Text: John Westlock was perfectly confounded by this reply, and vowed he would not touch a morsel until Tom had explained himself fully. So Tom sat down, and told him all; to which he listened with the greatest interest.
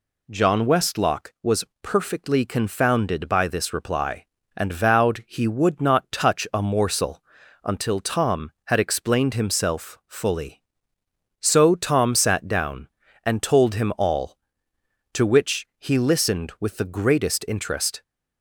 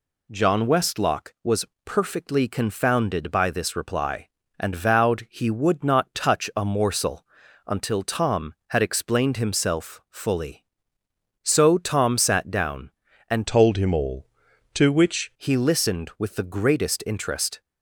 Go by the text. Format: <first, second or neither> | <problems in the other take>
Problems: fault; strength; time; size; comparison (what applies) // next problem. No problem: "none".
first | pauses between "was" and "perfectly"; slight; at 1.6 s; 0.20 s long; slight in the first // pauses between "morsel" and "until"; at 7.2 s; 0.42 s long; also in the first // changes voice from "told" to "which"; from 13.4 to 15.3 s; 1.9 s long